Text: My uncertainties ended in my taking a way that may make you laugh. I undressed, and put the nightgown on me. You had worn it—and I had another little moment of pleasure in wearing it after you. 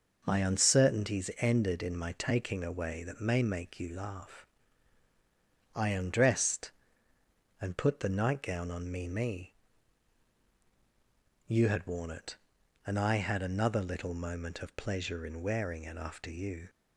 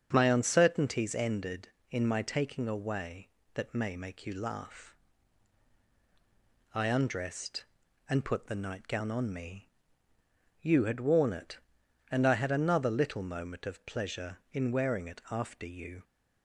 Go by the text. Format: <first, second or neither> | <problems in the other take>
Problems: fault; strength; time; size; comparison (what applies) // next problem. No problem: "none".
second | starts louder than the rest; noticeable; until 1.2 s; 6 dB; strong in the second // says "me" twice; at 9.0 s